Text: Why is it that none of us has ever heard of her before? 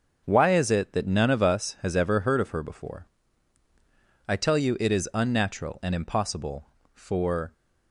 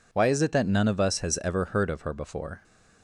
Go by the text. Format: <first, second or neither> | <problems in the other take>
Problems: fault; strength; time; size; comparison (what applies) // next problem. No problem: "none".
second | goes on to say "I tell you it is unnatural and impossible for"; strong; from 4.2 s on; 3.2 s long